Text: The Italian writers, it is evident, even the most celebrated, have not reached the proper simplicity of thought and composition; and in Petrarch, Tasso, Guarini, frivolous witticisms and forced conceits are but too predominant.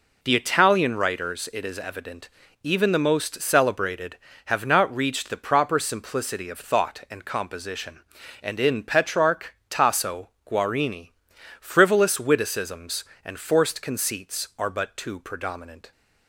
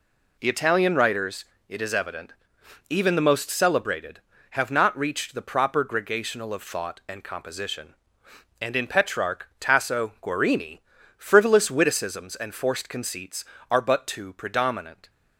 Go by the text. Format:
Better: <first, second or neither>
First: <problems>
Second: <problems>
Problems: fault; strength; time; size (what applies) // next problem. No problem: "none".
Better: first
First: none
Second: says "gregational" for "simplicity"; at 5.8 s